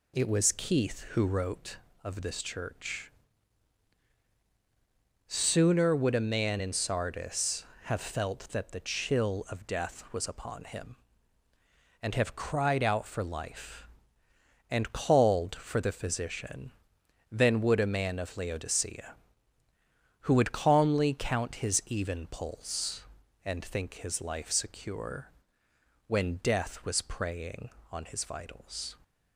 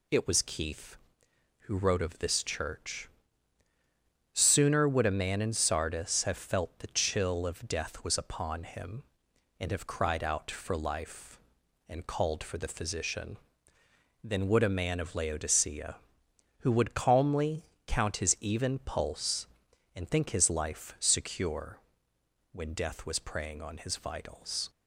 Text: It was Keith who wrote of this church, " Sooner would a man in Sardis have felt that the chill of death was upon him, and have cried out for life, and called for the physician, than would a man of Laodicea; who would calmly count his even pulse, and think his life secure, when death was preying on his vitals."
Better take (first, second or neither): first